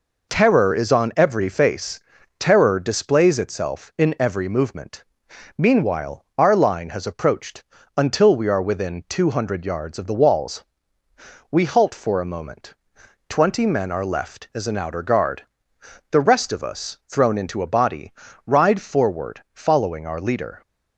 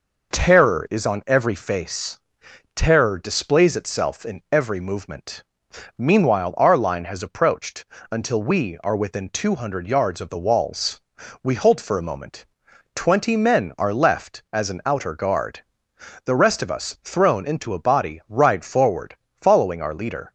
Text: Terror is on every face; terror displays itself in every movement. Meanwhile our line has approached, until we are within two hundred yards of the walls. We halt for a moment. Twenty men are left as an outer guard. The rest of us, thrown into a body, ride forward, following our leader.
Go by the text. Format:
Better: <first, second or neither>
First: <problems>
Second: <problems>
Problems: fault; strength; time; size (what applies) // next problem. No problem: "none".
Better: neither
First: none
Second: none